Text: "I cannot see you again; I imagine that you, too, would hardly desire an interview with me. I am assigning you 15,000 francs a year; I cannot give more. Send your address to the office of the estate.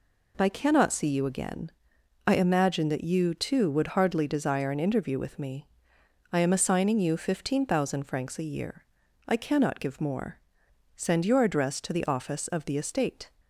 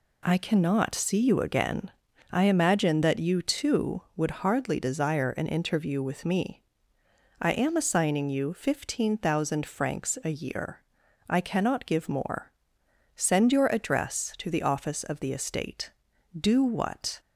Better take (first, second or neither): first